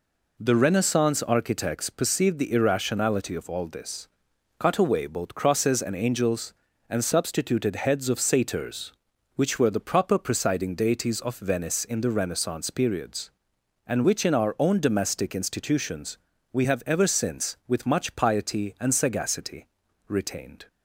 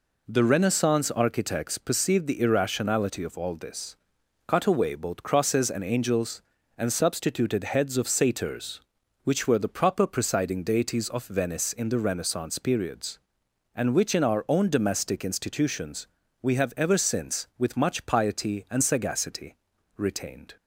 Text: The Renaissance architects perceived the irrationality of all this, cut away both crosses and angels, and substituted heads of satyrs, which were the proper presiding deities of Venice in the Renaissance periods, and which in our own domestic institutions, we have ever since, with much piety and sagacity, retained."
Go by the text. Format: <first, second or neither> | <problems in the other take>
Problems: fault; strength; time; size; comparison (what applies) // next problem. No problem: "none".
neither | none